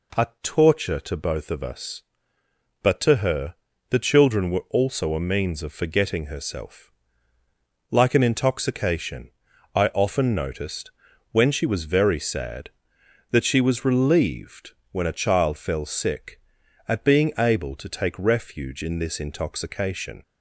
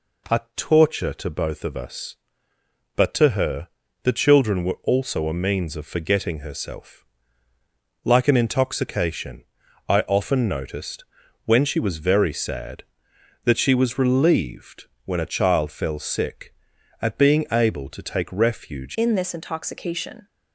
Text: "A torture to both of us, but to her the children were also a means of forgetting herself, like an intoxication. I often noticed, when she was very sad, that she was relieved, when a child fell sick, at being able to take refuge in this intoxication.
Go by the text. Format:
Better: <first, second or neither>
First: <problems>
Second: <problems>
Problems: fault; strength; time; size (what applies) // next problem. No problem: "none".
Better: first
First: pauses between "her" and "the"; slight; at 3.5 s; 0.34 s long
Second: pauses between "her" and "the"; slight; at 3.6 s; 0.34 s long // changes voice at "in"; from 18.9 s on; 1.3 s long